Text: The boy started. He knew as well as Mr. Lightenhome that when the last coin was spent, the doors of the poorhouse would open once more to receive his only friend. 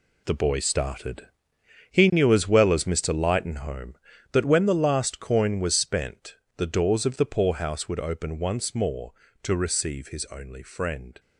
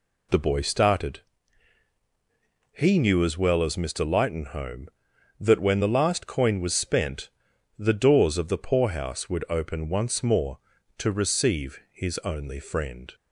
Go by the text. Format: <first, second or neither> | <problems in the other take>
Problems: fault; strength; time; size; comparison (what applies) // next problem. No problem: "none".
second | gets quieter; strong; throughout; 10.5 dB